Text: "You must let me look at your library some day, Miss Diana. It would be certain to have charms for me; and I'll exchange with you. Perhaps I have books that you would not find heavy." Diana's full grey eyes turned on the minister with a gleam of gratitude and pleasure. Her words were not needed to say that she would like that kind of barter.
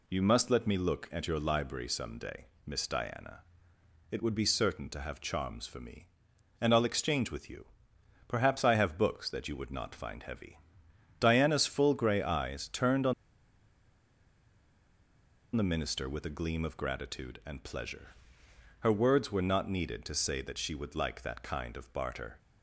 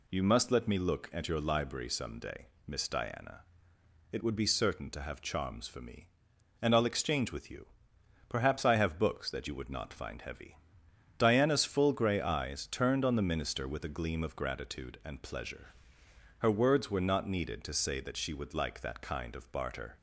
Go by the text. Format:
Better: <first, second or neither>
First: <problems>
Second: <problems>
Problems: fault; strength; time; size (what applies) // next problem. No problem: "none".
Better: second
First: pauses between "on" and "the"; strong; at 13.1 s; 2.4 s long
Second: none